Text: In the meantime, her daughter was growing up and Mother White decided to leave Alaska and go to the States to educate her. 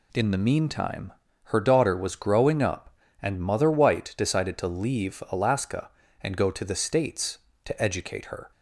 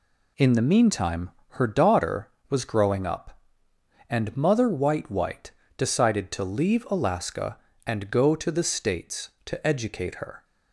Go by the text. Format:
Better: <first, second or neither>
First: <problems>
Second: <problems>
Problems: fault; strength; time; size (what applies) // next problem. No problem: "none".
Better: first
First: none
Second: says "White" twice; at 5.1 s